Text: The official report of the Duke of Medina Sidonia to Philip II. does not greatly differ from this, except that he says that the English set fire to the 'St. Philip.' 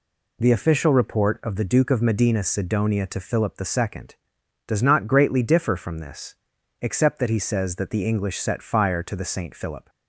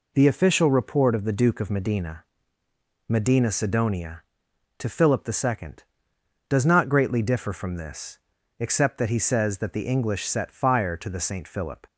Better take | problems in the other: first | says "Medina" twice; at 3.0 s

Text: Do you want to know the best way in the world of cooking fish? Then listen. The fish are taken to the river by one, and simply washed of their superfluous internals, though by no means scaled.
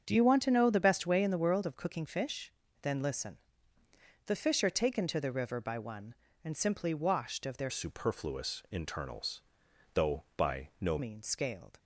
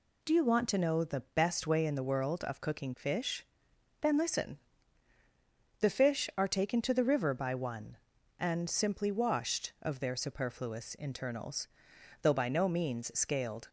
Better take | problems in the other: second | starts louder than the rest; until 1.0 s; 7 dB // changes voice from "superfluous" to "no"; from 7.6 to 10.9 s; 3.3 s long

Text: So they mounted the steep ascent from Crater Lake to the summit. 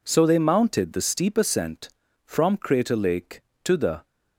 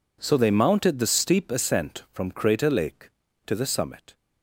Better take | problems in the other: second | stops before "summit"; at 4.0 s

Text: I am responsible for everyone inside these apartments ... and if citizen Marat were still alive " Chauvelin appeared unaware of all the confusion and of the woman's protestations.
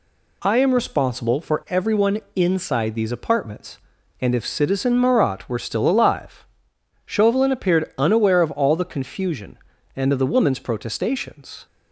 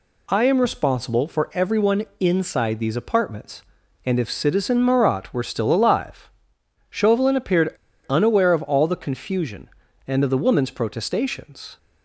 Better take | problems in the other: first | pauses between "everyone" and "inside"; slight; at 2.0 s; 0.16 s long; slight in the first // pauses between "appeared" and "unaware"; slight; at 7.7 s; 0.30 s long

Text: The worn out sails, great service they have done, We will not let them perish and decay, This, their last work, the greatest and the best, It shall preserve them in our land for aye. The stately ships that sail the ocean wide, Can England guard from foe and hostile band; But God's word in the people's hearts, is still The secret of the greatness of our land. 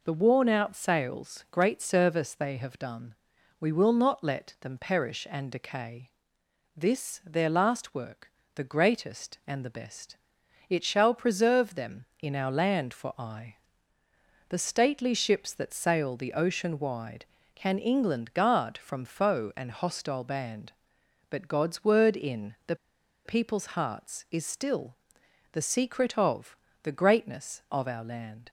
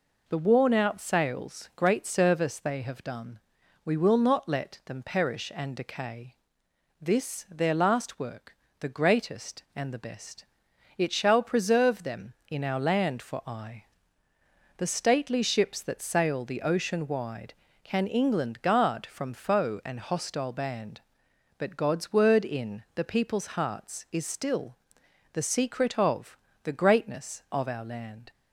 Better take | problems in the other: second | pauses between "the" and "people's"; noticeable; at 22.7 s; 0.49 s long // pauses between "still" and "The"; noticeable; at 24.9 s; 0.56 s long; noticeable in the second // pauses between "of" and "the"; slight; at 26.5 s; 0.26 s long; slight in the second

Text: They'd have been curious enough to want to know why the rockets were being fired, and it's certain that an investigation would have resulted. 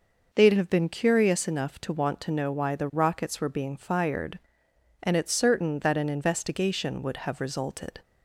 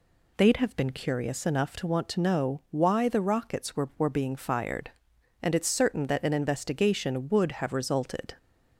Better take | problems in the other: first | says "were" twice; at 3.9 s

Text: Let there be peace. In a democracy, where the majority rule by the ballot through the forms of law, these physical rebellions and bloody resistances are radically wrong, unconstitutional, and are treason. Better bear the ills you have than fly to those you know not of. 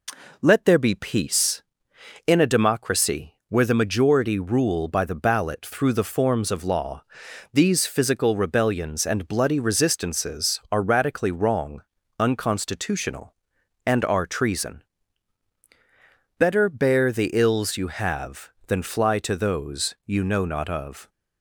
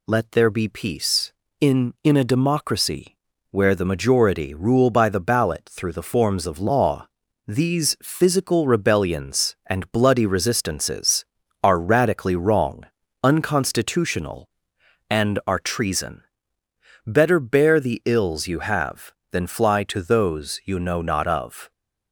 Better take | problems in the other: first | says "In" twice; at 2.0 s

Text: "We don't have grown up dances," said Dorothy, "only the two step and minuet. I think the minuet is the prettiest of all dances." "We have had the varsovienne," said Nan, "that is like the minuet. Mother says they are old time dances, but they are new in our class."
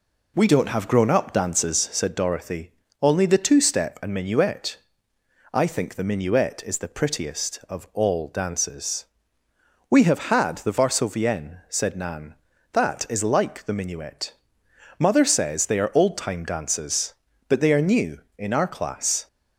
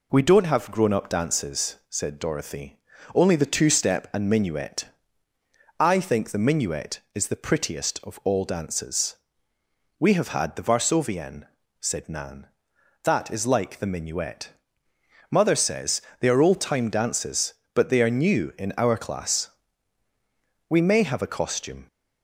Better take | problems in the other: first | pauses between "says" and "they"; slight; at 16.0 s; 0.18 s long // goes on to say "We may have a costume"; noticeable; from 20.6 s on; 1.1 s long

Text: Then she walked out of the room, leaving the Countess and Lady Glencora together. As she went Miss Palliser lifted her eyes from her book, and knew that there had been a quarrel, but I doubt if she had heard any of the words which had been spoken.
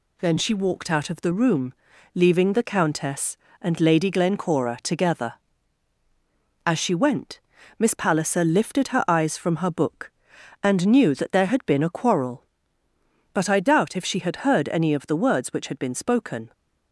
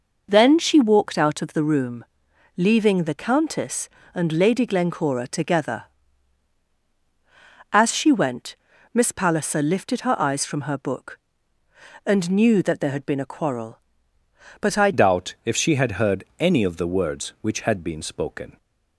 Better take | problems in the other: first | pauses between "went" and "Miss"; at 8.5 s; 0.38 s long; also in the first // changes voice at "doubt"; from 14.9 s on; 3.6 s long

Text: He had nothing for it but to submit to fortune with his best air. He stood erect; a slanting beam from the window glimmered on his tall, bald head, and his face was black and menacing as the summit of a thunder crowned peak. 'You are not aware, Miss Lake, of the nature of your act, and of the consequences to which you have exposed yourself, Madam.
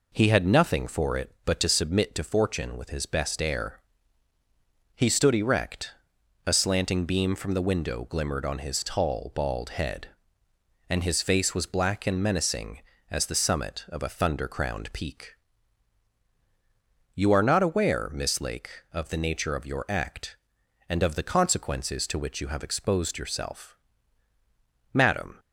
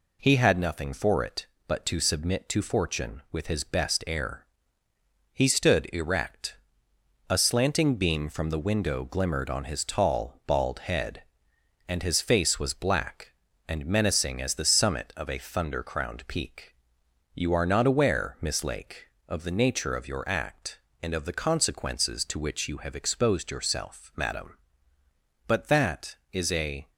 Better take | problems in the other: first | goes on to say "But that is a"; from 25.4 s on; 1.4 s long

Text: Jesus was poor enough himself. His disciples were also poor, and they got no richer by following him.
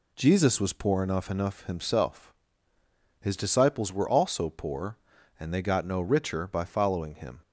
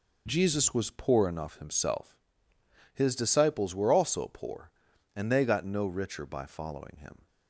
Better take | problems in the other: second | says "enough" twice; at 1.2 s

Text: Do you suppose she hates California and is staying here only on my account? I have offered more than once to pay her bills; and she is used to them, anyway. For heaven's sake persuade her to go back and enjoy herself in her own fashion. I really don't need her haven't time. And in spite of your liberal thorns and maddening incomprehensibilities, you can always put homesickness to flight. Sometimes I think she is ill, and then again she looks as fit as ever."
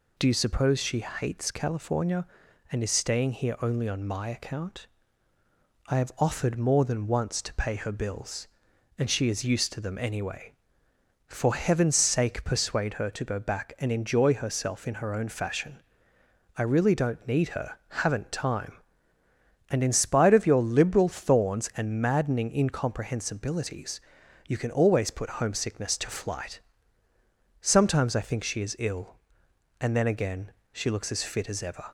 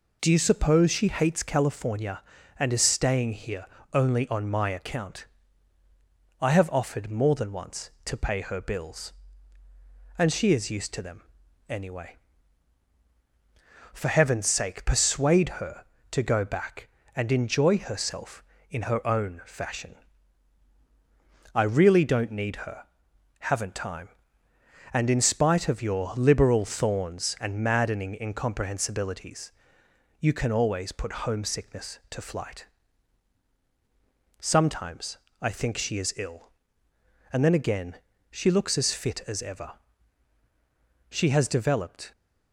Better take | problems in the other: first | pauses between "here" and "only"; slight; at 3.6 s; 0.28 s long // pauses between "her" and "haven't"; noticeable; at 22.8 s; 0.60 s long // pauses between "Sometimes" and "I"; slight; at 35.1 s; 0.22 s long // pauses between "again" and "she"; slight; at 37.9 s; 0.34 s long; slight in the first // goes on to say "She has developed"; noticeable; from 41.0 s on; 1.0 s long

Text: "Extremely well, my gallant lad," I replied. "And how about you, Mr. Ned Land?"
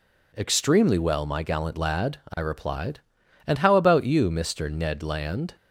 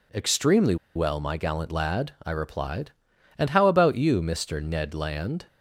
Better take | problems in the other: first | pauses between "Extremely" and "well"; slight; at 0.7 s; 0.20 s long

